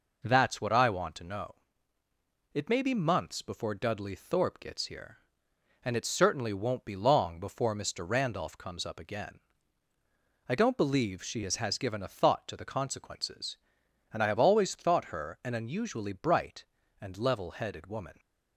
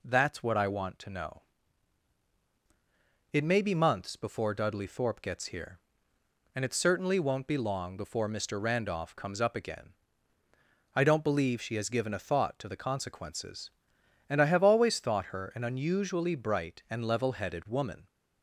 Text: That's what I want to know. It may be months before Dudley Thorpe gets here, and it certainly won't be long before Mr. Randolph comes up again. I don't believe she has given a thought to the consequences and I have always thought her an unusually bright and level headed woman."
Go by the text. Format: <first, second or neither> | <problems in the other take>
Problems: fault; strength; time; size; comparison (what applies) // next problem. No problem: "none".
second | says "has" twice; at 11.5 s